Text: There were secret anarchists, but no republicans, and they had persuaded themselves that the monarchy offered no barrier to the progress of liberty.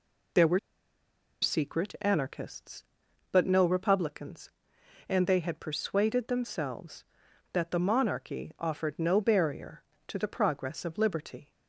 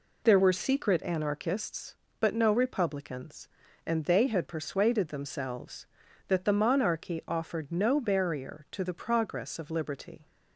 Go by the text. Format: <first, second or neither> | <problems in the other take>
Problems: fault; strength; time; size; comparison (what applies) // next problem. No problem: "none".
second | pauses between "were" and "secret"; noticeable; at 0.5 s; 0.83 s long